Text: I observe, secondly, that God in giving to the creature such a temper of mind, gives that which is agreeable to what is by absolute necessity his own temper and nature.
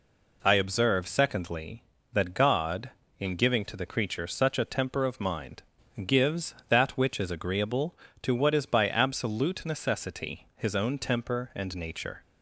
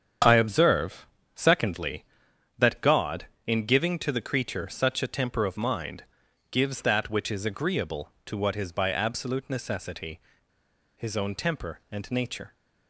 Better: first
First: none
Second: starts louder than the rest; strong; until 1.5 s; 8 dB // pauses between "necessity" and "his"; noticeable; at 10.2 s; 0.74 s long

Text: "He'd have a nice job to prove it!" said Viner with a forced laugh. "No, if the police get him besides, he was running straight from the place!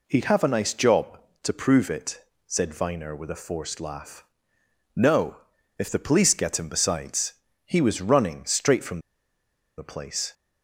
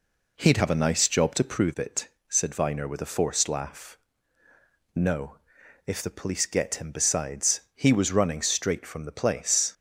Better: second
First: pauses between "from" and "the"; noticeable; at 8.9 s; 0.78 s long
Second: none

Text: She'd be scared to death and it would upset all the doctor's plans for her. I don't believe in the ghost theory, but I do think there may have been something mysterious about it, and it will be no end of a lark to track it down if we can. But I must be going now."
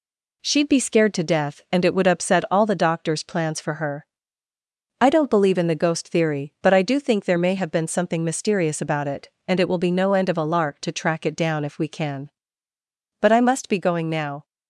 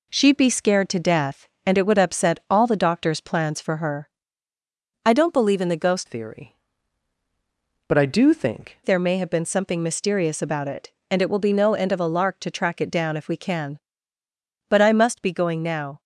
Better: first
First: none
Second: changes voice from "theory" to "think"; from 6.0 to 8.7 s; 2.7 s long

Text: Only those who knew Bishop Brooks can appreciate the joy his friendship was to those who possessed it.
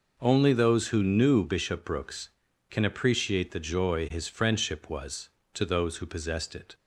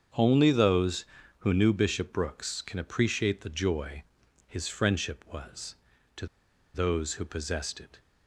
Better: first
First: none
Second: starts louder than the rest; strong; until 1.5 s; 7.5 dB // pauses between "joy" and "his"; at 4.0 s; 0.42 s long // pauses between "to" and "those"; noticeable; at 6.2 s; 0.48 s long

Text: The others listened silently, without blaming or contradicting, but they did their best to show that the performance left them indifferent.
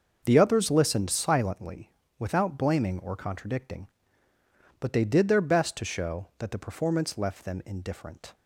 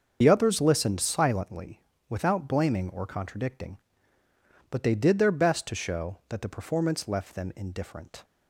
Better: first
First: starts louder than the rest; until 1.2 s; 6.5 dB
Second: loses the start of "The"; at 0.2 s; 55 ms // starts louder than the rest; until 1.2 s; 6.5 dB

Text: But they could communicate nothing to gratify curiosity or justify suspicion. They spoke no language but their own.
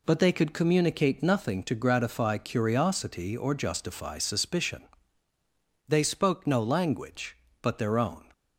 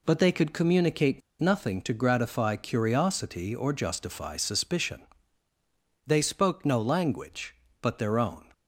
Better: first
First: none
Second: pauses between "communicate" and "nothing"; slight; at 1.2 s; 0.20 s long

